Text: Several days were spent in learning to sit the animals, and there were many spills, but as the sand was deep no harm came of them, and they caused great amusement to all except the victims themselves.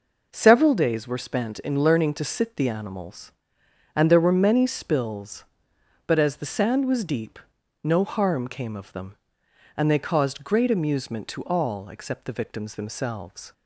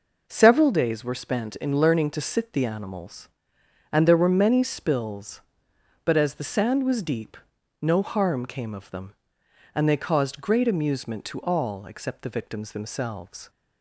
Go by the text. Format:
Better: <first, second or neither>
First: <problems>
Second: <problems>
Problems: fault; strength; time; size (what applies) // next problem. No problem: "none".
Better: neither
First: pauses between "deep" and "no"; at 7.3 s; 0.44 s long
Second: pauses between "deep" and "no"; at 7.3 s; 0.44 s long